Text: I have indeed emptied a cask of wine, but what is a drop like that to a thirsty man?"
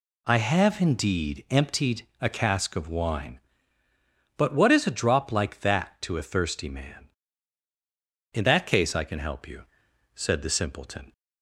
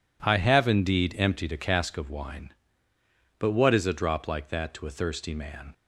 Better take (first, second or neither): second